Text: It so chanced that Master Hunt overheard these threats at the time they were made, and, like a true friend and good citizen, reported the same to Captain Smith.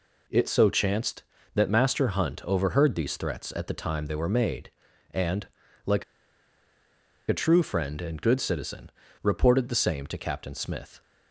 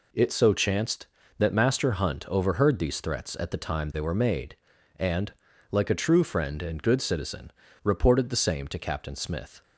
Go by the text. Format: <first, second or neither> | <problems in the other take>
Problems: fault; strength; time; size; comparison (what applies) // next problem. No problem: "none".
second | pauses between "like" and "a"; strong; at 6.0 s; 1.2 s long